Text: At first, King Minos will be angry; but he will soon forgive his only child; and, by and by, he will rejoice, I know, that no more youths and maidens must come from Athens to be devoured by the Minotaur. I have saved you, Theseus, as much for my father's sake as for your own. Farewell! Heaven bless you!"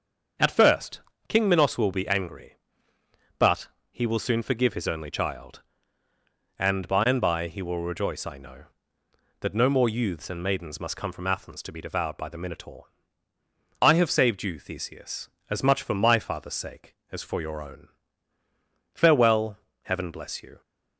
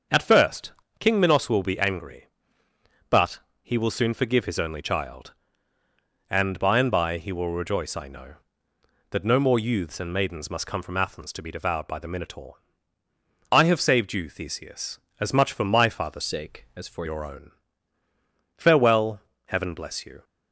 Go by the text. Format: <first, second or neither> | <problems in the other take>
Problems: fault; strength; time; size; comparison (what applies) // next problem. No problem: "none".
first | starts louder than the rest; until 1.3 s; 7 dB; also in the first // pauses between "but" and "he"; slight; at 3.4 s; 0.22 s long; slight in the first // changes voice from "sake" to "for"; from 16.2 to 17.0 s; 0.8 s long